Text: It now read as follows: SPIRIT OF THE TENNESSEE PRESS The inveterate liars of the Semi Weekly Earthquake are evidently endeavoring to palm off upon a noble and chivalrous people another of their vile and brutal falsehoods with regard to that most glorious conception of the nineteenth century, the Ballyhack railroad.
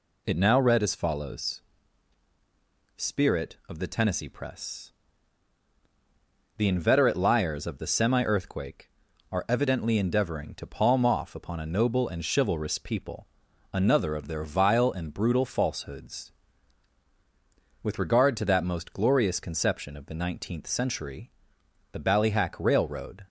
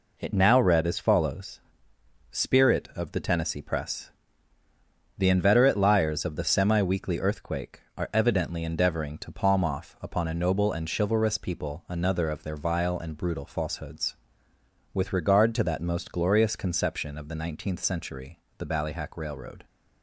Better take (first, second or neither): second